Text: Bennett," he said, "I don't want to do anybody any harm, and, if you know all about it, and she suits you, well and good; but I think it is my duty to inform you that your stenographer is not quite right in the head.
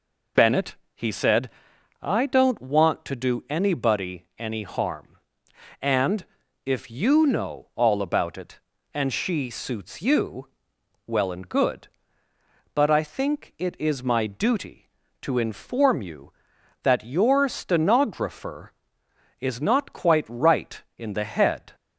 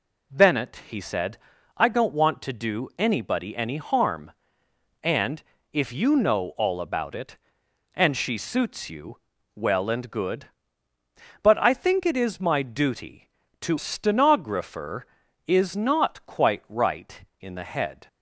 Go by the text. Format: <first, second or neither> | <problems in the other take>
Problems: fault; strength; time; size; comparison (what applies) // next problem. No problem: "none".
first | skips "inform you that your"; at 13.7 s